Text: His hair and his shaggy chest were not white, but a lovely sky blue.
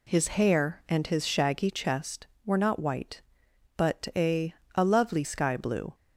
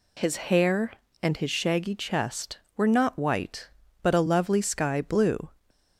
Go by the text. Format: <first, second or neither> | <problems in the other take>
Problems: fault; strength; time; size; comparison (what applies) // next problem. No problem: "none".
second | says "a" twice; at 4.7 s